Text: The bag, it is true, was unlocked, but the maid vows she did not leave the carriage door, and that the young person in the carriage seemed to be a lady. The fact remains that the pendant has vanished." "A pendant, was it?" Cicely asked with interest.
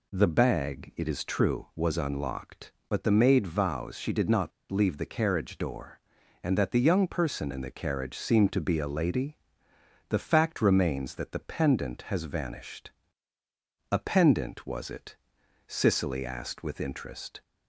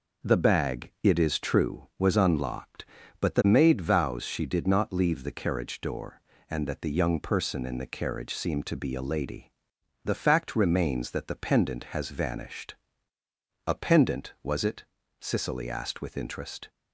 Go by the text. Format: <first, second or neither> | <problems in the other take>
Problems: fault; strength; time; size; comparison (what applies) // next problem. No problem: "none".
second | pauses between "not" and "leave"; slight; at 4.5 s; 0.20 s long